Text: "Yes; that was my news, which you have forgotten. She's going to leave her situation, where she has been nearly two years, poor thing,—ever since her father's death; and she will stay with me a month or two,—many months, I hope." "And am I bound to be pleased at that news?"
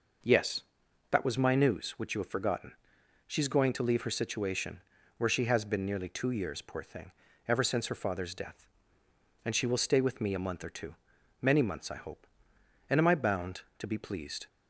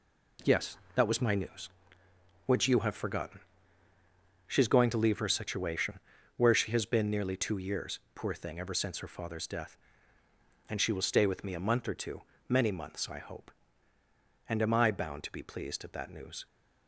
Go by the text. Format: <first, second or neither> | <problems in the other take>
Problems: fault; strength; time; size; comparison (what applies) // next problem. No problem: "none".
second | stops before "at that news"; at 14.4 s